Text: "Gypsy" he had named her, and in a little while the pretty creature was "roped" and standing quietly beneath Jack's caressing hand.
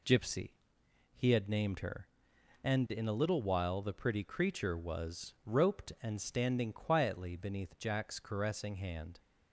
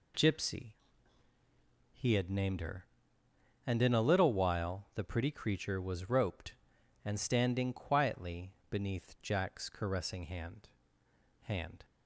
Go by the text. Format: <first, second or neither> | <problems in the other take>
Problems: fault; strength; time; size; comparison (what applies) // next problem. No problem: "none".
first | pauses between "Gypsy" and "he"; at 0.7 s; 1.2 s long; noticeable in the first // pauses between "quietly" and "beneath"; slight; at 8.5 s; 0.16 s long // says "hand" twice; at 11.4 s